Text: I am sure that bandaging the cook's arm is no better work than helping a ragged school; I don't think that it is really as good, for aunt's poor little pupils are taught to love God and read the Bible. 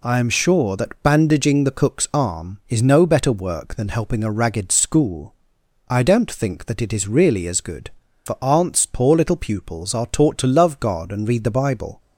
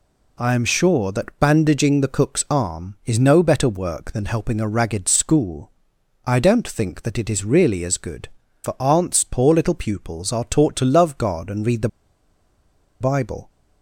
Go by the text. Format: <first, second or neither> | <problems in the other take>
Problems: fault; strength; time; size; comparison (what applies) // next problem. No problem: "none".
first | pauses between "the" and "Bible"; at 11.8 s; 1.1 s long